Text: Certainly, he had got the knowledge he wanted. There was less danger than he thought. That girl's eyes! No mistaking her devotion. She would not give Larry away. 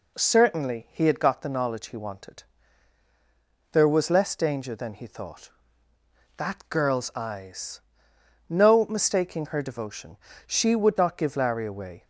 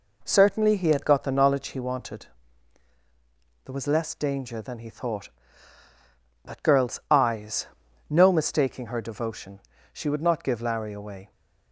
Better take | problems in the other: neither | none

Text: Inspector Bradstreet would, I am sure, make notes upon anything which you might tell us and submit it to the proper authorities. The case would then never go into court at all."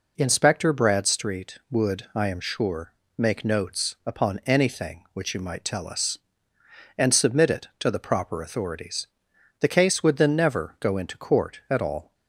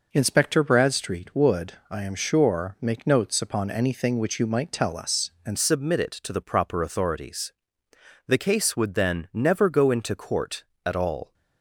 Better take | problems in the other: first | changes voice at "submit"; from 5.5 s on; 5.8 s long

